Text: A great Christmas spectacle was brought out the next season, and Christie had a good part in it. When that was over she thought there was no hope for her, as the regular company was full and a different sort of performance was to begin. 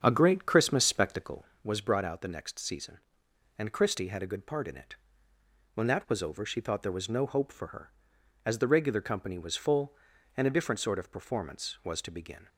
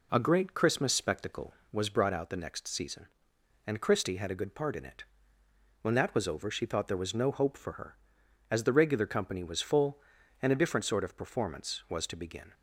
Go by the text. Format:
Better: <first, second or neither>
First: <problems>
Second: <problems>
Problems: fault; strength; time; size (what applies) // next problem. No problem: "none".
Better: second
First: starts louder than the rest; strong; until 1.3 s; 7.5 dB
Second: none